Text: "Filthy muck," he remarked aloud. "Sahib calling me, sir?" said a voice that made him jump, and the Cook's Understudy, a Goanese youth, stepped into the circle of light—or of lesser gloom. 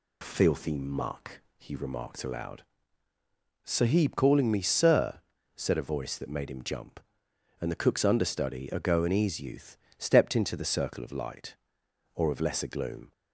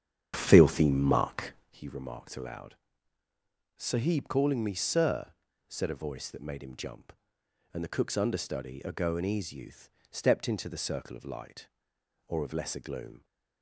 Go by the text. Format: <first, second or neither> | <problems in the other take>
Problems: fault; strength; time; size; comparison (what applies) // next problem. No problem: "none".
first | starts louder than the rest; strong; until 1.8 s; 9 dB